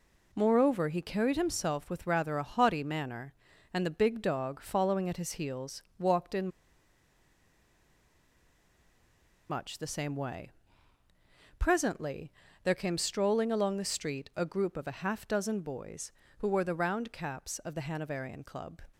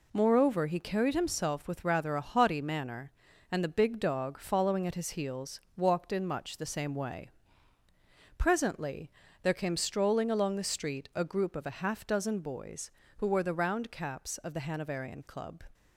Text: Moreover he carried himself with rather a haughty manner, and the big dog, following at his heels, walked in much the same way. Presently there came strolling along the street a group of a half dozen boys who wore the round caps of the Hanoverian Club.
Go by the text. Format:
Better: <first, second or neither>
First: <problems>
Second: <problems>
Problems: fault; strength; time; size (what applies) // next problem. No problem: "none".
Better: second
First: pauses between "in" and "much"; strong; at 6.4 s; 3.0 s long // pauses between "Presently" and "there"; slight; at 12.3 s; 0.34 s long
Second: pauses between "Presently" and "there"; slight; at 9.0 s; 0.34 s long